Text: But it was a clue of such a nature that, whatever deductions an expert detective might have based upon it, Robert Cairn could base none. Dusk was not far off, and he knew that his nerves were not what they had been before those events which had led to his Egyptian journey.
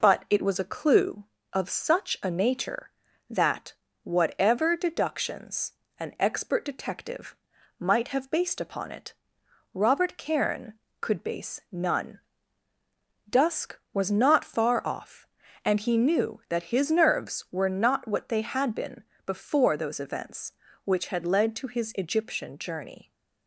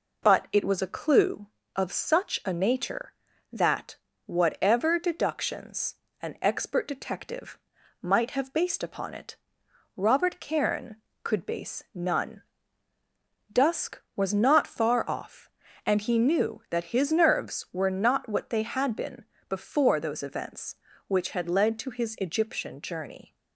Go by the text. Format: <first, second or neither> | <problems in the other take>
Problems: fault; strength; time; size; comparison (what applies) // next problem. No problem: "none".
neither | pauses between "deductions" and "an"; slight; the same in both // pauses between "detective" and "might"; the same in both // pauses between "been" and "before"; slight; the same in both